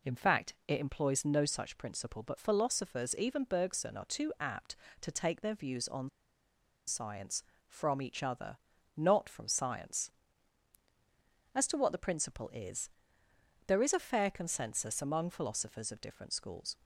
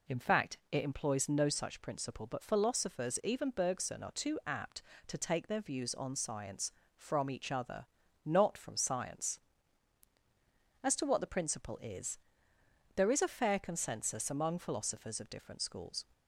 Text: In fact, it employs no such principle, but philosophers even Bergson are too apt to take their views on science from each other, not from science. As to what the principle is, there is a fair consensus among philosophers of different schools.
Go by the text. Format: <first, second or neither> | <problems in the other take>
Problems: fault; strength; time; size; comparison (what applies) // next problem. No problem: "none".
second | pauses between "on" and "science"; noticeable; at 6.0 s; 0.78 s long